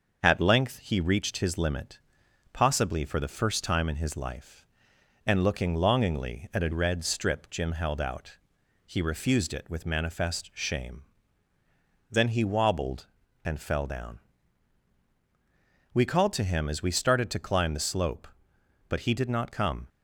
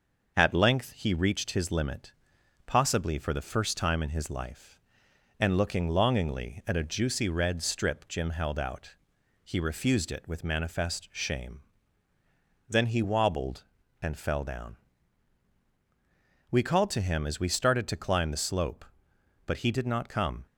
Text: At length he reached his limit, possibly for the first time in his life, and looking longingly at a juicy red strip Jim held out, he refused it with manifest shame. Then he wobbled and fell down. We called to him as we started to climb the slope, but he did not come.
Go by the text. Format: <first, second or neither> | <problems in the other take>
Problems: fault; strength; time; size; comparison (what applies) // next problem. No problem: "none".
second | starts louder than the rest; until 1.2 s; 6.5 dB; noticeable in the second // skips "juicy"; at 6.7 s